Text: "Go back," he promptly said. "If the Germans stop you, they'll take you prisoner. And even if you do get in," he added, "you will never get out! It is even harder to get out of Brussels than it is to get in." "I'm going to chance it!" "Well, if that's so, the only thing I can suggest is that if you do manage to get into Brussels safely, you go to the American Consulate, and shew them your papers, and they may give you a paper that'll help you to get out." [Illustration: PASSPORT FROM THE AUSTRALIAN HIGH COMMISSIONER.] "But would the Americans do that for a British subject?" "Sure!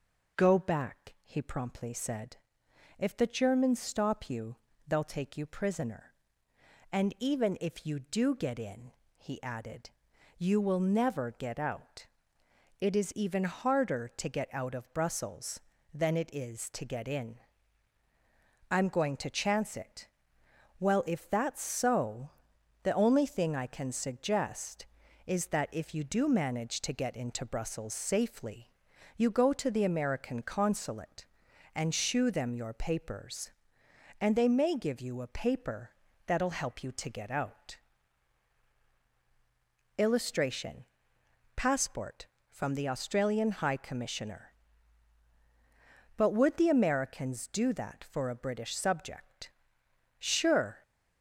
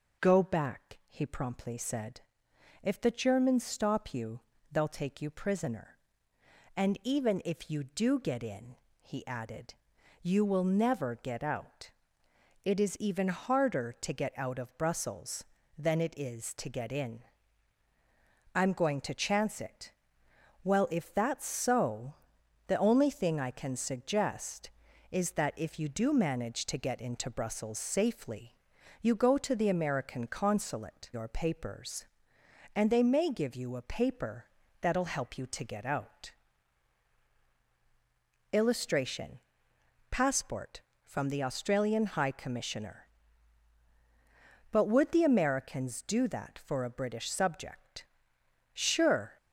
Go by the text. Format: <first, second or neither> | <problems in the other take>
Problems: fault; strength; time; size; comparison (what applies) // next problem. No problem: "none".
first | skips "and shew them"; at 31.1 s // pauses between "paper" and "that'll"; slight; at 34.4 s; 0.34 s long; slight in the first